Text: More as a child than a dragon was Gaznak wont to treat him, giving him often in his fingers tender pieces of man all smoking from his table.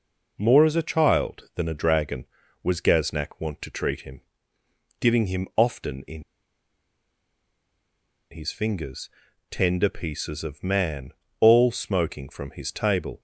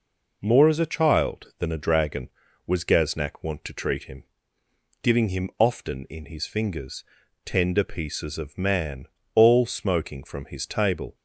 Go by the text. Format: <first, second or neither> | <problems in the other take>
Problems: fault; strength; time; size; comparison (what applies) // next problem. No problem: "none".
second | pauses between "in" and "his"; strong; at 6.2 s; 2.0 s long // pauses between "fingers" and "tender"; at 9.1 s; 0.40 s long; also in the second // pauses between "man" and "all"; slight; at 11.1 s; 0.30 s long; slight in the second